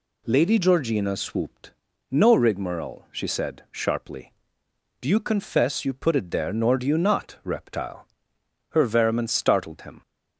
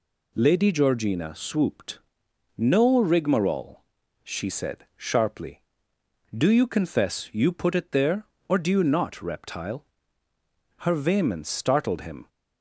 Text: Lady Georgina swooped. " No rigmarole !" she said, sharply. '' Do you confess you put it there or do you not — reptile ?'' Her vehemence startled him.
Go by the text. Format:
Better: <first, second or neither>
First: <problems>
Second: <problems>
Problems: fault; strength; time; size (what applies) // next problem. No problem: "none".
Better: second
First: says "nor" for "or"; at 6.5 s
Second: none